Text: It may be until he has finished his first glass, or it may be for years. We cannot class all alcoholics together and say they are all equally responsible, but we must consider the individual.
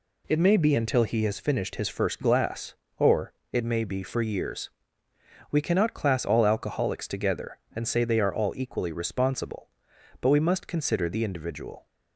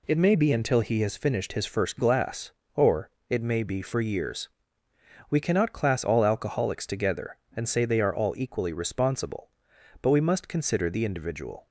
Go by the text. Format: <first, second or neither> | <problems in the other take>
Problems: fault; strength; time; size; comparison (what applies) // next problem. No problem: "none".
neither | pauses between "or" and "it"; slight; the same in both